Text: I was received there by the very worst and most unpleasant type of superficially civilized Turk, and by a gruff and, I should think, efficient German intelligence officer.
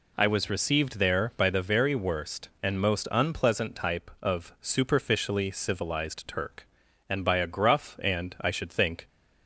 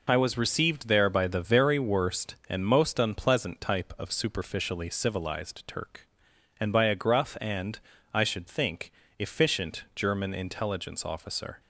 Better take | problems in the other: second | stops before "efficient German intelligence officer"; at 9.0 s

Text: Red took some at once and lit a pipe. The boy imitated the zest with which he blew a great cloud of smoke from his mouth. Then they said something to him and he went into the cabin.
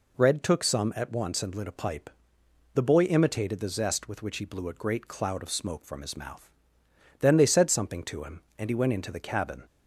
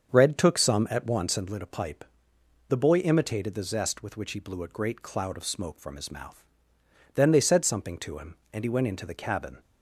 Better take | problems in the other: first | starts louder than the rest; until 1.6 s; 7 dB

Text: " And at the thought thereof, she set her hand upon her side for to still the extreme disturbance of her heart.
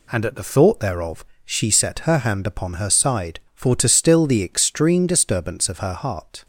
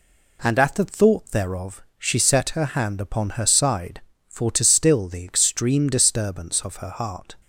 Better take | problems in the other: neither | none

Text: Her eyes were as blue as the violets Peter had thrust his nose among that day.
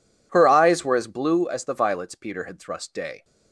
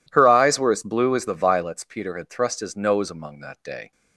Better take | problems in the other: second | skips "his nose among that"; at 2.9 s

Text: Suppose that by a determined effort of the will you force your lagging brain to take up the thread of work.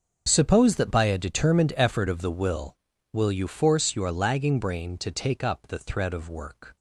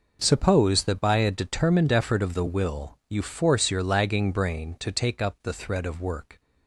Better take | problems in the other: second | starts louder than the rest; until 1.2 s; 7 dB // says "will" twice; at 3.1 s

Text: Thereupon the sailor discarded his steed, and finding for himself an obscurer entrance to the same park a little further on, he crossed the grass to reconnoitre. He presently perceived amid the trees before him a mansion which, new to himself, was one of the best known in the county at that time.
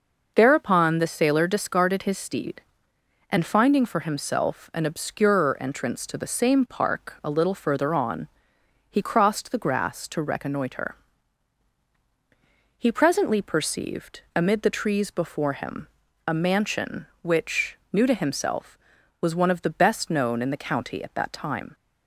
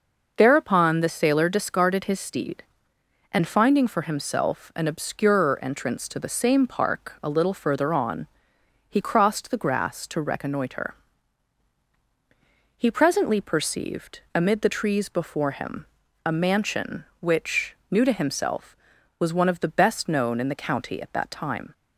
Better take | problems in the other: neither | pauses between "him" and "a"; the same in both

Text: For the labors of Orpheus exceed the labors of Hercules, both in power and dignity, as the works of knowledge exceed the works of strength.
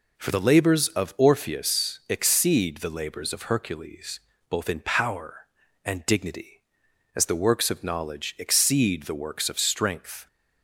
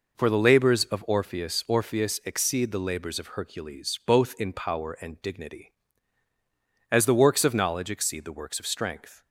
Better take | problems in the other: first | says "Orpheus" twice; at 1.6 s

